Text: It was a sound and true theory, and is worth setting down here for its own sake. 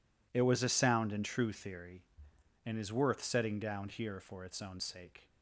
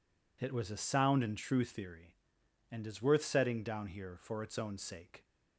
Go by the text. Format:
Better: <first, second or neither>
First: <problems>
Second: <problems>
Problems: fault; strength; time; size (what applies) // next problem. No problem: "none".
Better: neither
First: none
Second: none